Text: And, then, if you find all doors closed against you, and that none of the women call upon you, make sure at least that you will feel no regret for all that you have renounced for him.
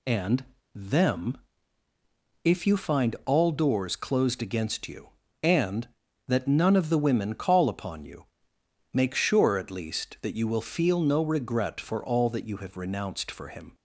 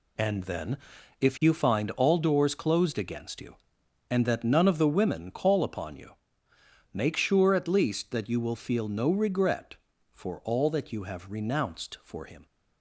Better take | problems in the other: second | says "them" for "then"; at 0.7 s

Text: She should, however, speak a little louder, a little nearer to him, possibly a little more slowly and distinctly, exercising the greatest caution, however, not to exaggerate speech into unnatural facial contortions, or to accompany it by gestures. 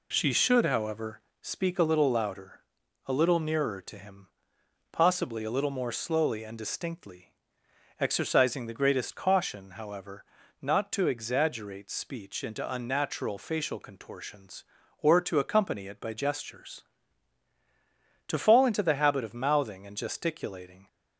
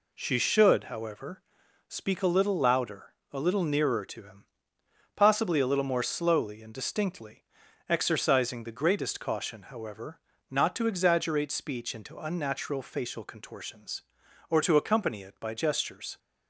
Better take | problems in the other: second | goes on to say "To fall into the habit of mouthing and gesticulating"; strong; from 18.2 s on; 2.6 s long

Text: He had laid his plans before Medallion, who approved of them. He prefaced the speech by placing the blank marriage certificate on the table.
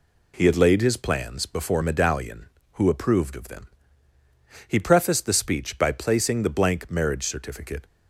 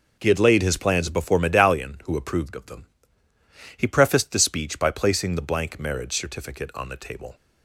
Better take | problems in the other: second | stops before "on the table"; at 7.8 s

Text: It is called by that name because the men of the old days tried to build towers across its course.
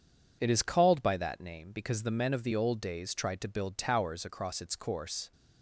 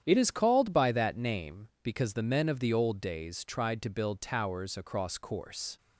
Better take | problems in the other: first | starts louder than the rest; strong; until 1.0 s; 9.5 dB // skips "its"; at 5.1 s

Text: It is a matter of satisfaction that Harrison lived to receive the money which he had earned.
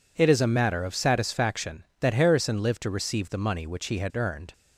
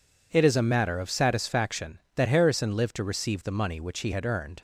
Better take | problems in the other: neither | none

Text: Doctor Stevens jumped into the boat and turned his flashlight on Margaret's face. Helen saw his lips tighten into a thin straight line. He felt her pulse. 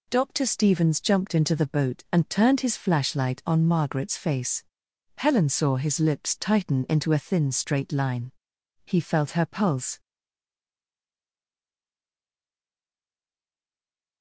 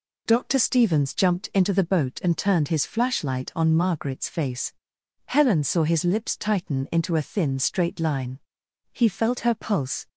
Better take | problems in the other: second | stays silent after the last word; strong; from 9.9 s on; 4.3 s long

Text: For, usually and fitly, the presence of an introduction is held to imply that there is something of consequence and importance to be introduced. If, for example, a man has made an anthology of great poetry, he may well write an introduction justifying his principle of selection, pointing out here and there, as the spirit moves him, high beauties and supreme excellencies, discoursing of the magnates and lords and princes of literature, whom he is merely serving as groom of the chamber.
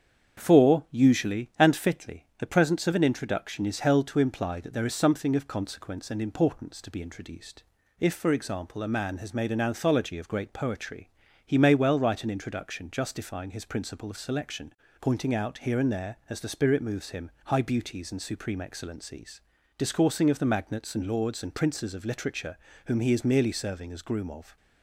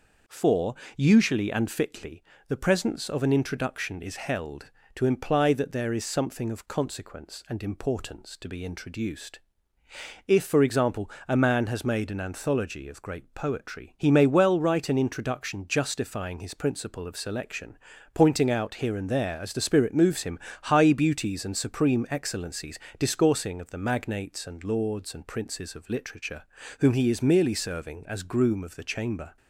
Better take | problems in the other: second | starts louder than the rest; strong; until 1.4 s; 7.5 dB // stops before "the chamber"; at 24.5 s

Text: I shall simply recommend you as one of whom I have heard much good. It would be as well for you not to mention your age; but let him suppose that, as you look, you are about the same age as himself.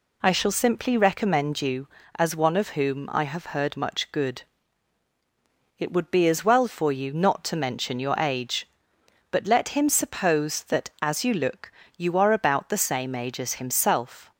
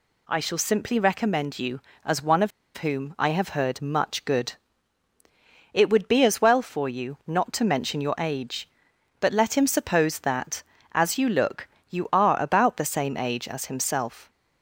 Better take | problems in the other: first | pauses between "of" and "whom"; slight; at 2.5 s; 0.26 s long

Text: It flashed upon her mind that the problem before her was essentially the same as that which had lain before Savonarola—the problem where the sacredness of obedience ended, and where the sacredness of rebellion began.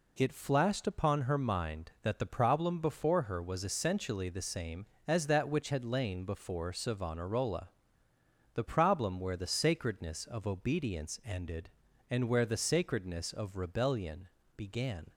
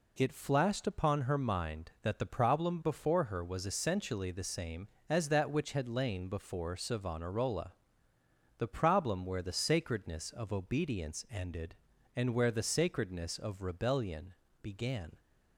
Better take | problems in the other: neither | pauses between "rebellion" and "began"; slight; the same in both

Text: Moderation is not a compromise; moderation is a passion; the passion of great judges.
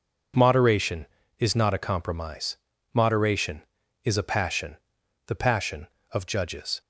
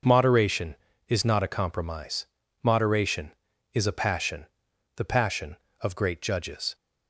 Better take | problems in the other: second | skips "great"; at 6.2 s

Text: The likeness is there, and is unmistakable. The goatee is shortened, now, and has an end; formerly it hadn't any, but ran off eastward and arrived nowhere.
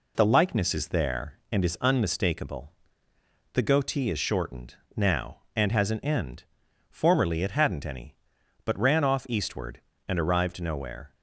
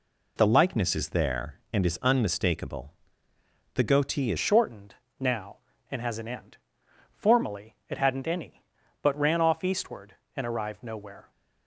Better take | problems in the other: first | changes voice at "shortened"; from 4.3 s on; 7.0 s long

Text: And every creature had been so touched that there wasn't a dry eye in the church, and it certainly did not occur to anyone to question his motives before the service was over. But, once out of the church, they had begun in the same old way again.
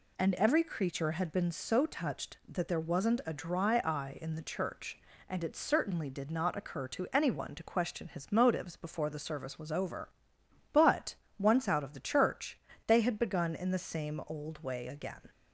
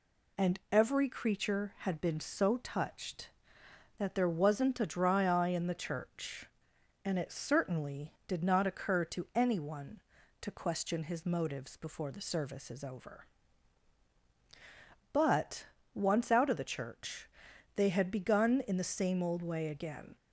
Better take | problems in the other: first | says "is" for "was"; at 12.7 s

